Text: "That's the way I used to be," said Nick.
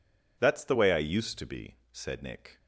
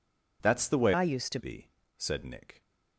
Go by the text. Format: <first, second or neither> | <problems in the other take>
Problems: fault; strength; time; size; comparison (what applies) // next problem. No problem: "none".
first | changes voice from "I" to "to"; from 0.9 to 1.3 s; 0.4 s long